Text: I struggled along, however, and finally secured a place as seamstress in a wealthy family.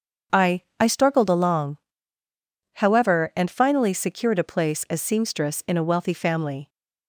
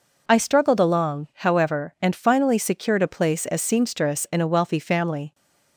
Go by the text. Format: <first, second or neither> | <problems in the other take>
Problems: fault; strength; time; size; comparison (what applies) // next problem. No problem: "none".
second | starts louder than the rest; strong; until 1.4 s; 7 dB // says "I" twice; at 0.7 s